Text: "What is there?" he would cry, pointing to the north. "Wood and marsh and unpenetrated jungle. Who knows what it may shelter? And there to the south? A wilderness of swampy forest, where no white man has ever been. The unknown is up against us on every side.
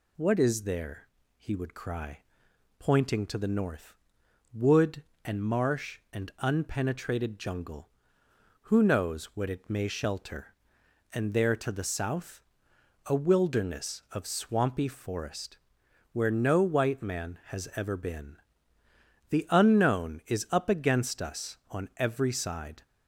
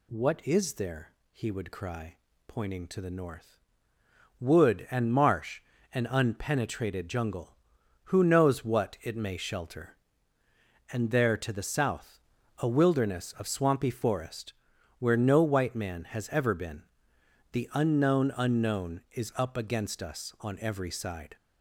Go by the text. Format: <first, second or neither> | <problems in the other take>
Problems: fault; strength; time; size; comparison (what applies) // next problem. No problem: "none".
first | says "unknown" twice; at 18.3 s